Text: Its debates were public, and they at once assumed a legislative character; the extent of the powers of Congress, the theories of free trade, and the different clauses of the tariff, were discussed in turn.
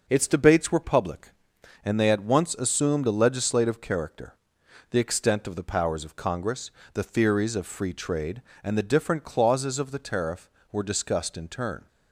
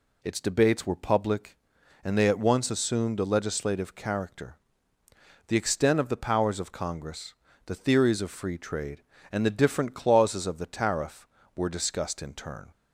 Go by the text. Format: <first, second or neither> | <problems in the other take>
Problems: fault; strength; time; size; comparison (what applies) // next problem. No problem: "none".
neither | none